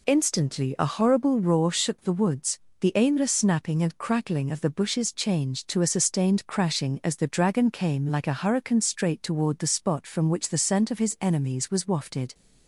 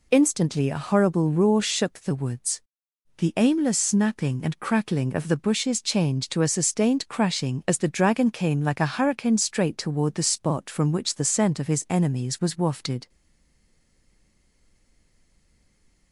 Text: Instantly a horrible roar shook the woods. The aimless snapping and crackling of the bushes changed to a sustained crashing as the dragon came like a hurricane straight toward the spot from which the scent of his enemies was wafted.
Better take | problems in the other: first | stays silent after the last word; strong; from 13.0 s on; 3.1 s long

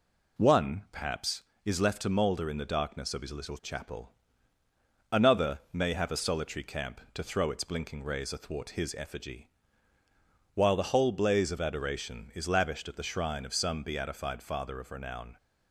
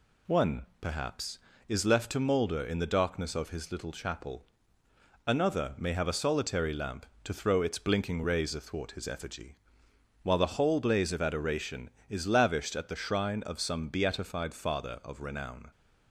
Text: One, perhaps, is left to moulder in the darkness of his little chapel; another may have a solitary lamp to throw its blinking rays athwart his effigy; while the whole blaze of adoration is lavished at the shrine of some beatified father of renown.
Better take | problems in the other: second | says "camp" for "lamp"; at 6.6 s

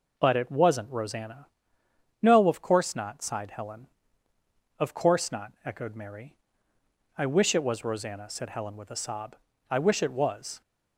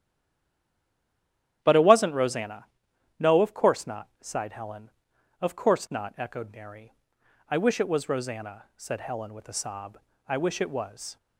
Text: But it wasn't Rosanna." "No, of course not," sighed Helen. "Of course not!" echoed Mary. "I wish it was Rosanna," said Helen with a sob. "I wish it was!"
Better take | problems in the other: first | stays silent before the first word; noticeable; until 1.6 s; 1.6 s long // starts louder than the rest; strong; until 2.6 s; 11 dB

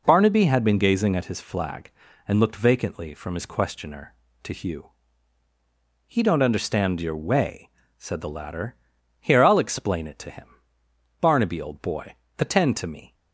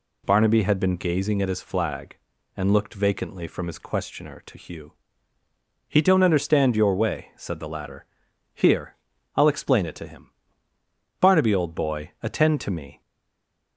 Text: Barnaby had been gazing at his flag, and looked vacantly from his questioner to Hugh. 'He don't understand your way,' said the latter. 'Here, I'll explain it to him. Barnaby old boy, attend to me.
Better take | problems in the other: first | stays silent after the last word; slight; from 13.0 s on; 0.7 s long

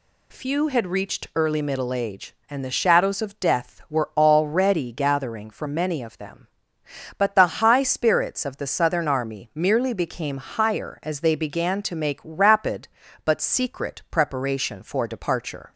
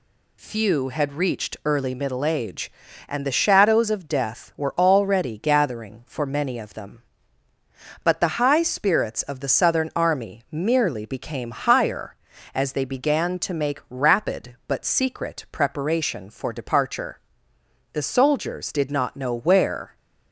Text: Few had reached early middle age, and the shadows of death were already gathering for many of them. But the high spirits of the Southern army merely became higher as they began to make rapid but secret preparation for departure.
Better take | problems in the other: first | goes on to say "The soldiers did not know where"; strong; from 17.9 s on; 2.0 s long

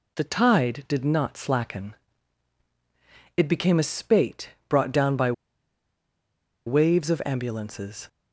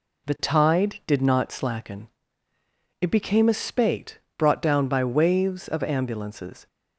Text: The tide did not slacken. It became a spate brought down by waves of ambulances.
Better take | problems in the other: second | pauses between "spate" and "brought"; slight; at 4.5 s; 0.18 s long; slight in the second // pauses between "by" and "waves"; strong; at 5.3 s; 1.3 s long

